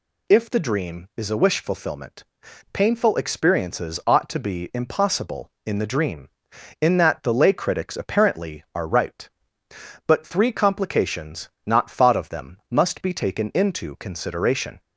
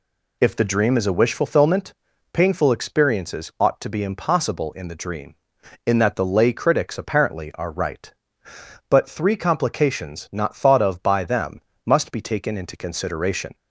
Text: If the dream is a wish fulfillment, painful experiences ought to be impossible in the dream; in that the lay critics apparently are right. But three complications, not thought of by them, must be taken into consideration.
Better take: second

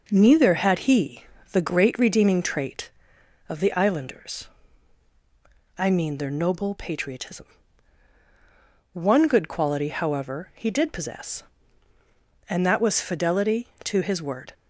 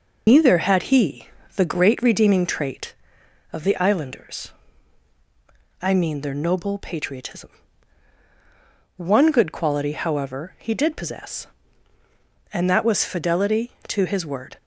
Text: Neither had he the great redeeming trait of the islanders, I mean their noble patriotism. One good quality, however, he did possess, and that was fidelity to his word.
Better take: first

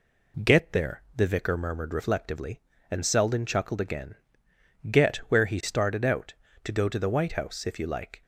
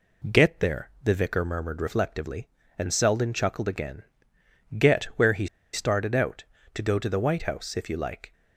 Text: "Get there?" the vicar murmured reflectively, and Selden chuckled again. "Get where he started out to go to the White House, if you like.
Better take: first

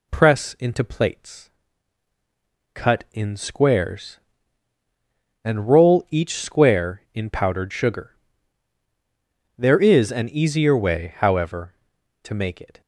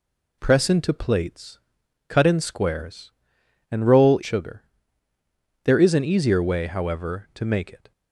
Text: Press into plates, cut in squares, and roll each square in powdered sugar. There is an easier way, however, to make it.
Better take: first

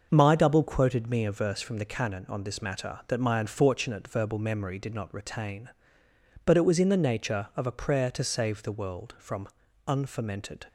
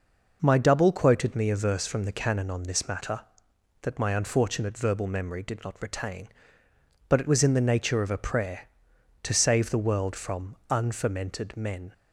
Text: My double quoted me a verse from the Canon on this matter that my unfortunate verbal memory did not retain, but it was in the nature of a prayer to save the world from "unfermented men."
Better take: second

